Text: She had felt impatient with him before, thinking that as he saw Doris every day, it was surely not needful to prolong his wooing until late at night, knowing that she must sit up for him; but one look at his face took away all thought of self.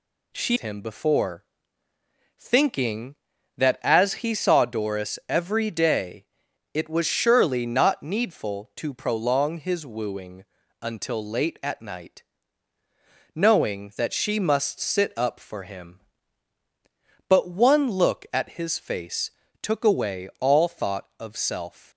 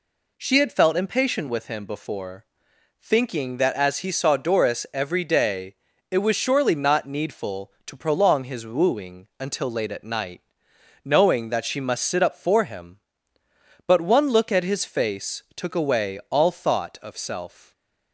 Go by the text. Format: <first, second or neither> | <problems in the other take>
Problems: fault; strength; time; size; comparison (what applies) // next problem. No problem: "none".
second | skips "had felt impatient with"; at 0.5 s // pauses between "wooing" and "until"; slight; at 10.4 s; 0.36 s long // pauses between "face" and "took"; slight; at 19.3 s; 0.30 s long